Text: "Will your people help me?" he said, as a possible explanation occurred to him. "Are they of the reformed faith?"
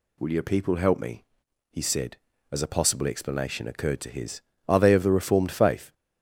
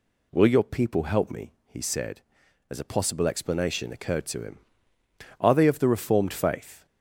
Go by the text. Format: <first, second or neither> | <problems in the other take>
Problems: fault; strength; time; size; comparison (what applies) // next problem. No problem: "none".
second | says "his" for "him"; at 4.0 s